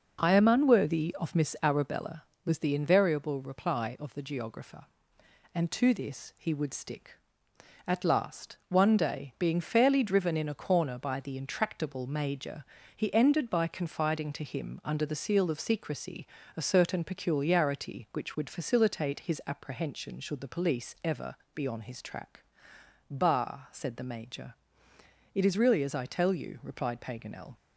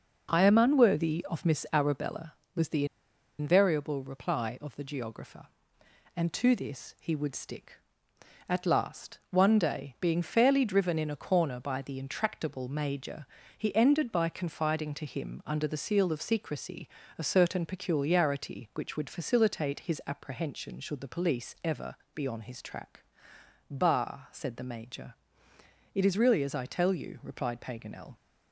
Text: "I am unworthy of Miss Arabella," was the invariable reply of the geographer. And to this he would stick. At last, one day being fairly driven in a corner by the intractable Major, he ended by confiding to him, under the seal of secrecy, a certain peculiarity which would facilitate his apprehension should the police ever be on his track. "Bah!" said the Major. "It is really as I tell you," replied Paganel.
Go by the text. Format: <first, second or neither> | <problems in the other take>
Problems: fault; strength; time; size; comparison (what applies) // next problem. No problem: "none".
first | pauses between "the" and "invariable"; noticeable; at 2.8 s; 0.53 s long // pauses between "ever" and "be"; slight; at 21.9 s; 0.22 s long; slight in the first